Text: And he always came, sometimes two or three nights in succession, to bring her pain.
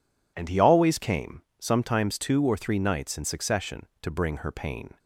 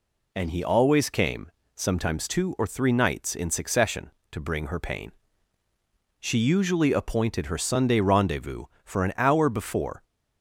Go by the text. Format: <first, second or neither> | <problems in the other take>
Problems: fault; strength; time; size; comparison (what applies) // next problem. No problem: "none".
first | goes on to say "She usually appointed her Sunday rendezvous for an hour before"; strong; from 6.1 s on; 3.8 s long